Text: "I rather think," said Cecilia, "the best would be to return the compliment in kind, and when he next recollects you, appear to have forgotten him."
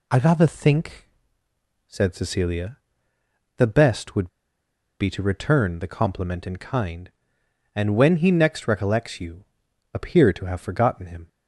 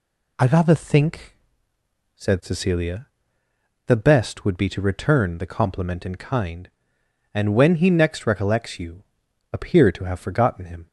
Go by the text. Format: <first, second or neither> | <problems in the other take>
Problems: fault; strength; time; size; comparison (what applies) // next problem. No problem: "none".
second | pauses between "would" and "be"; noticeable; at 4.2 s; 0.72 s long